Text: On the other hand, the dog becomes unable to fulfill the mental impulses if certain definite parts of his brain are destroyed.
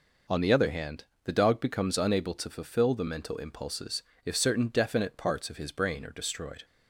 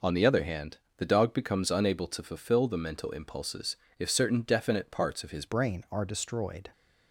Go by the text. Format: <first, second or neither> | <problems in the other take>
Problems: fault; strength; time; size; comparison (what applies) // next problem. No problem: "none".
first | pauses between "impulses" and "if"; slight; at 3.7 s; 0.22 s long; slight in the first // changes voice at "brain"; from 5.4 s on; 1.2 s long